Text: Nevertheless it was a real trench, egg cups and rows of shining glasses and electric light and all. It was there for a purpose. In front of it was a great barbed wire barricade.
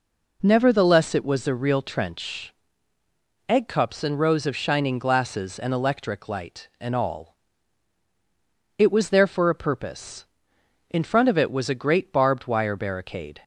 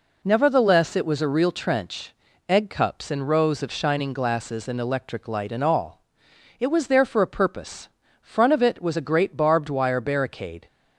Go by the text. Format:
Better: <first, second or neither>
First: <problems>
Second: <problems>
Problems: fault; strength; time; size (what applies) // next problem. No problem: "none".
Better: first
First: none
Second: skips "In"; at 8.0 s